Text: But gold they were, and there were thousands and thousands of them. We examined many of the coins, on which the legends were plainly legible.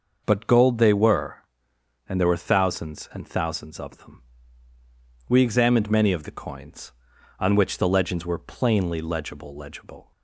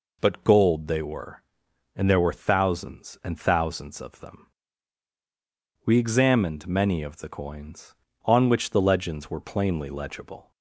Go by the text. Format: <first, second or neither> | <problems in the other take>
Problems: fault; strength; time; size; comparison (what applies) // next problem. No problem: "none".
second | says "legible" twice; at 9.5 s